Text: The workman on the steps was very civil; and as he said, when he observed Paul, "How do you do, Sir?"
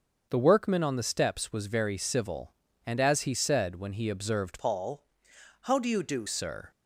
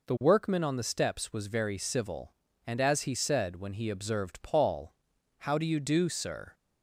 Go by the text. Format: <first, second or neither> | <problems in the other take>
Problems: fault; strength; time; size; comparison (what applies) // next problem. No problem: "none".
second | starts louder than the rest; until 1.3 s; 6.5 dB // changes voice from "Paul" to "do"; from 4.5 to 6.2 s; 1.7 s long